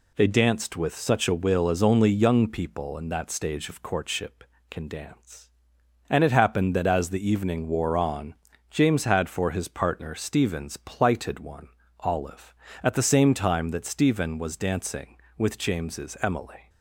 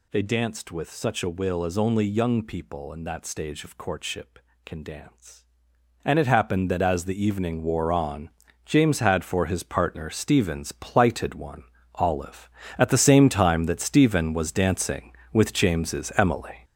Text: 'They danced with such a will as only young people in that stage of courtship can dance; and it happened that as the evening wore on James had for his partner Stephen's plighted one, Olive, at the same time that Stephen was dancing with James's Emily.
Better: first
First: pauses between "on" and "James"; slight; at 8.3 s; 0.34 s long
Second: gets louder; throughout; 7 dB // pauses between "on" and "James"; slight; at 8.3 s; 0.34 s long

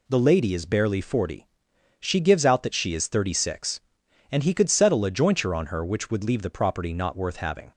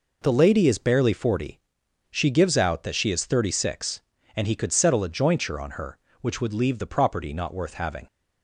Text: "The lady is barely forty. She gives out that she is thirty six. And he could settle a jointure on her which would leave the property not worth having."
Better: neither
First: none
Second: none

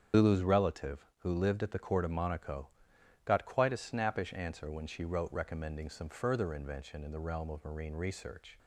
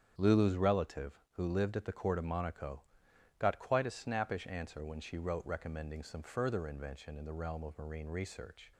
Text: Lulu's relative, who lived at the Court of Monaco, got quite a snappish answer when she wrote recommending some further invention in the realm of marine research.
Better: second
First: loses the start of "Lulu's"; at 0.1 s; 100 ms // starts louder than the rest; strong; until 1.2 s; 8 dB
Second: starts louder than the rest; strong; until 1.1 s; 8.5 dB

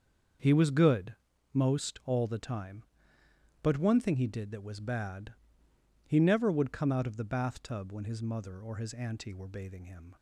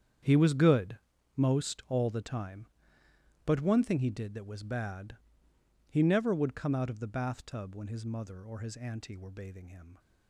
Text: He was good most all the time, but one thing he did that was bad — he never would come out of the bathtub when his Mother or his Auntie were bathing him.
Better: first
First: starts louder than the rest; until 1.7 s; 6.5 dB // pauses between "good" and "most"; at 1.1 s; 0.38 s long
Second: gets quieter; strong; throughout; 15 dB // starts louder than the rest; strong; until 1.6 s; 8.5 dB // pauses between "good" and "most"; at 0.9 s; 0.38 s long

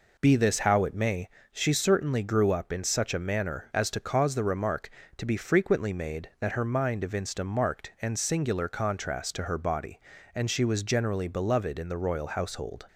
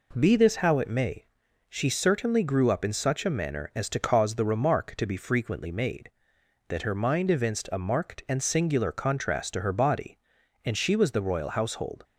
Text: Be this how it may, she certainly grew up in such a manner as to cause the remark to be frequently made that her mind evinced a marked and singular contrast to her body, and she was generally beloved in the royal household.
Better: first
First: none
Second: skips "generally beloved in"; at 11.1 s

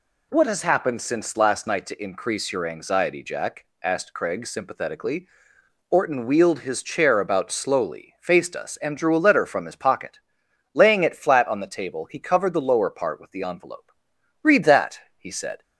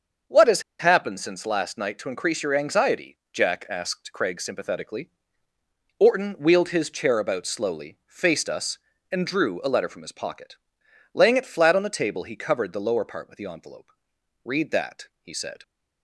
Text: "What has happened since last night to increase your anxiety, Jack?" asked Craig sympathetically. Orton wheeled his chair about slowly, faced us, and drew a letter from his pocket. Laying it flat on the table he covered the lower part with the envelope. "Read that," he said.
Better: first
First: none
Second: starts louder than the rest; until 1.4 s; 6.5 dB // pauses between "has" and "happened"; slight; at 0.6 s; 0.17 s long

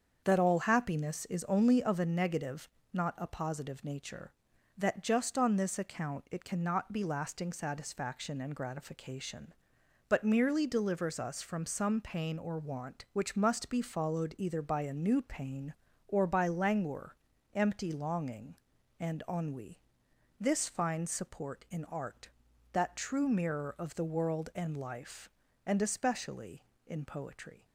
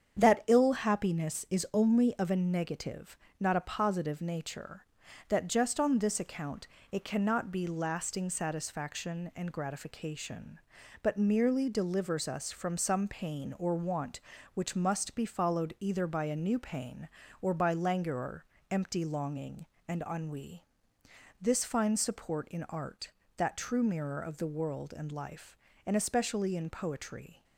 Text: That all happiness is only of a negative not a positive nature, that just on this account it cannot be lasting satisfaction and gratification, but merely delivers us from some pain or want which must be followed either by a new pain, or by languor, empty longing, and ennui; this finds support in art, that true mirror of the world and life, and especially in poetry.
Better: first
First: starts louder than the rest; until 1.2 s; 7 dB // pauses between "negative" and "not"; slight; at 2.6 s; 0.26 s long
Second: starts louder than the rest; strong; until 1.2 s; 8 dB // says "ill" for "all"; at 0.4 s // pauses between "negative" and "not"; slight; at 3.1 s; 0.22 s long // pauses between "account" and "it"; slight; at 6.6 s; 0.24 s long

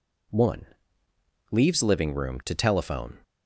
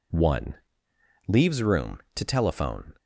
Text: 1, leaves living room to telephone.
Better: first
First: none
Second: skips "living"; at 1.6 s

